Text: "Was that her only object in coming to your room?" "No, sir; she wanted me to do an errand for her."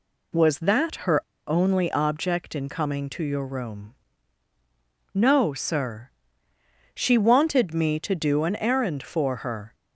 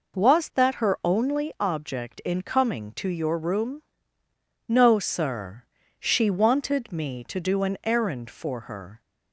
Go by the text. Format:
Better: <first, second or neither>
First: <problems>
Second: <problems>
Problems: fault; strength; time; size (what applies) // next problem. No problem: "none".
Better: second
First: pauses between "her" and "only"; slight; at 1.2 s; 0.23 s long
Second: none